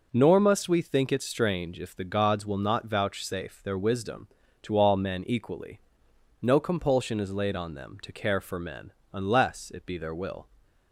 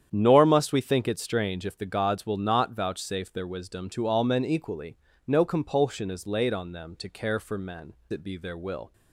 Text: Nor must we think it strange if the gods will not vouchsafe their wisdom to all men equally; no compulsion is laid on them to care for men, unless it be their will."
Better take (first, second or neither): first